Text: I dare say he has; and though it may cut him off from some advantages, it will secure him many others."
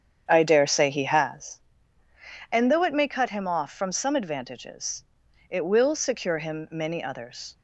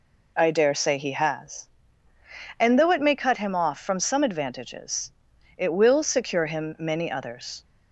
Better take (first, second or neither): second